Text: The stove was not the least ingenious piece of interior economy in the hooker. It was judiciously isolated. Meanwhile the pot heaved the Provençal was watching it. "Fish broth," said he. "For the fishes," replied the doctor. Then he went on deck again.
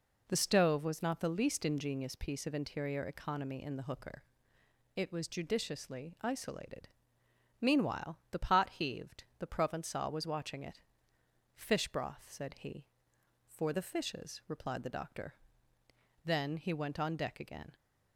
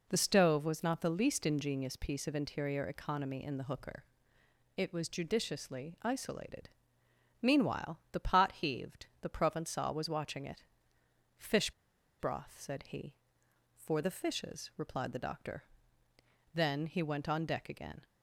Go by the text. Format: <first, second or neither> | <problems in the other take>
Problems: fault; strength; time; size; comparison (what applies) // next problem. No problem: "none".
first | pauses between "Fish" and "broth"; noticeable; at 11.7 s; 0.48 s long